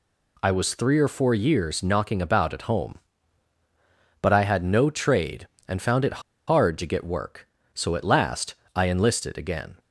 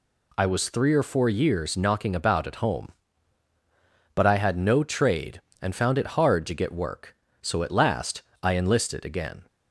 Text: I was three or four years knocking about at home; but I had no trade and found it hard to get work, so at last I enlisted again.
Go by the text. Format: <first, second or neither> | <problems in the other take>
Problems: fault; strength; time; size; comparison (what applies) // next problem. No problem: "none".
second | pauses between "it" and "hard"; slight; at 6.2 s; 0.25 s long // pauses between "last" and "I"; slight; at 8.5 s; 0.18 s long; slight in the second